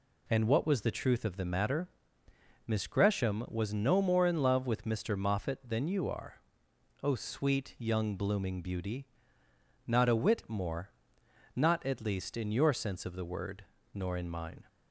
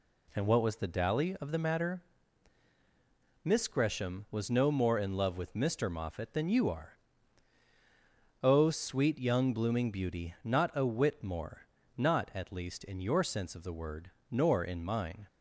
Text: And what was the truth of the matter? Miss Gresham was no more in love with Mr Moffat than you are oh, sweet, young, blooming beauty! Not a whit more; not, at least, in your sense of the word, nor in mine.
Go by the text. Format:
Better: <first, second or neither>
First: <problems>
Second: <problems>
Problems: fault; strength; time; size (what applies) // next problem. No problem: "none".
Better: first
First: pauses between "are" and "oh"; noticeable; at 6.3 s; 0.68 s long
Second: says "dally" for "truth"; at 0.8 s // pauses between "are" and "oh"; strong; at 6.9 s; 1.4 s long